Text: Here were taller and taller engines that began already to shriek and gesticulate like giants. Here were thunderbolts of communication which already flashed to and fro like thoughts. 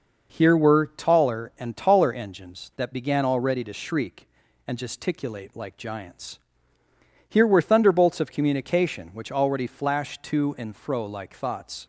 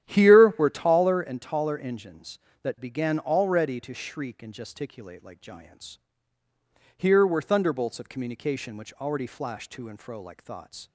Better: first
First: none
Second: starts louder than the rest; strong; until 1.3 s; 11.5 dB

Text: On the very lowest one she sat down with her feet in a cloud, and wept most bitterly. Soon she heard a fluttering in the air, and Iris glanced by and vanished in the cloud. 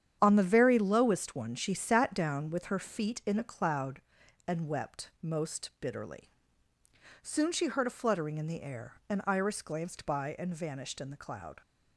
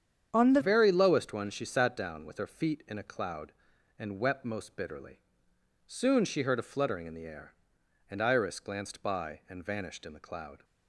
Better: first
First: starts louder than the rest; strong; until 1.2 s; 9.5 dB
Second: starts louder than the rest; strong; until 1.3 s; 8.5 dB // changes voice at "very"; from 0.6 s on; 10.0 s long

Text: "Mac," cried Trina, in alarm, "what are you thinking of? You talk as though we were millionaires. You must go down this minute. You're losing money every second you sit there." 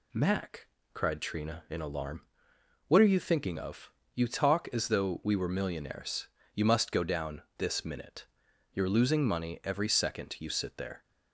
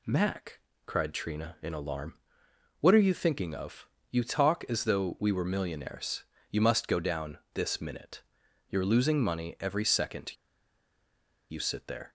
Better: first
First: none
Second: pauses between "second" and "you"; at 10.3 s; 1.1 s long

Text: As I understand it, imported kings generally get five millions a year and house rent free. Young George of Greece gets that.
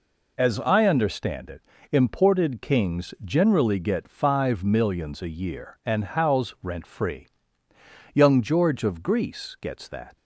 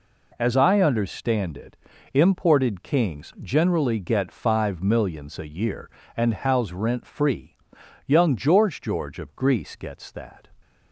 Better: first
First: none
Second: says "George" twice; at 8.8 s

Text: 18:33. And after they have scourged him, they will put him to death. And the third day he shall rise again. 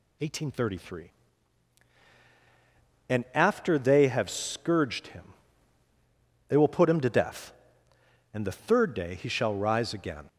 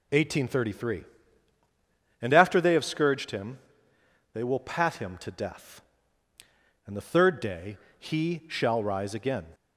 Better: first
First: none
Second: says "pat" for "put"; at 4.5 s // pauses between "day" and "he"; slight; at 7.7 s; 0.22 s long

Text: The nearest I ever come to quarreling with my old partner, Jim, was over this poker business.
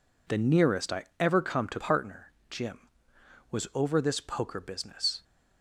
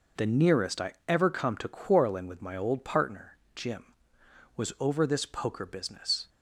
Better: second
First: pauses between "I" and "ever"; slight; at 1.0 s; 0.16 s long // skips "quarreling with my old"; at 1.7 s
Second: pauses between "I" and "ever"; slight; at 0.9 s; 0.16 s long

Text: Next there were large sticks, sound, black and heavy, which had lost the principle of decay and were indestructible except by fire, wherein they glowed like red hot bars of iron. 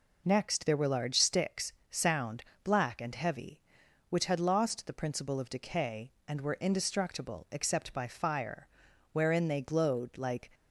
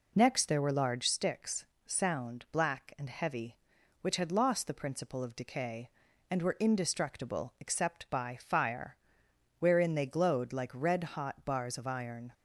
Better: second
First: stops before "red hot bars of iron"; at 10.5 s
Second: none

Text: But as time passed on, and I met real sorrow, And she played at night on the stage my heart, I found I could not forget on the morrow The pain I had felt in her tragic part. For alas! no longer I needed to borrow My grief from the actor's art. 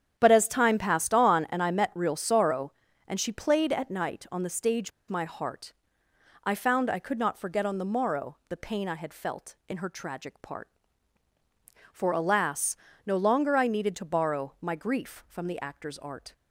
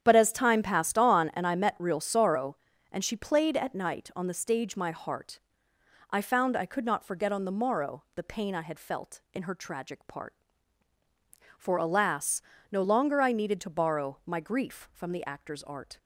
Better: second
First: starts louder than the rest; strong; until 1.1 s; 9 dB // pauses between "stage" and "my"; slight; at 4.9 s; 0.18 s long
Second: starts louder than the rest; strong; until 1.0 s; 9 dB

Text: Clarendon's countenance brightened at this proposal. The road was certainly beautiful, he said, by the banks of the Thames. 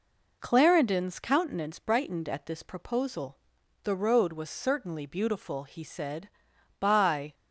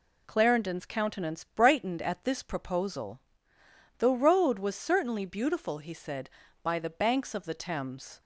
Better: second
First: stops before "the banks of the Thames"; at 7.3 s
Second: none

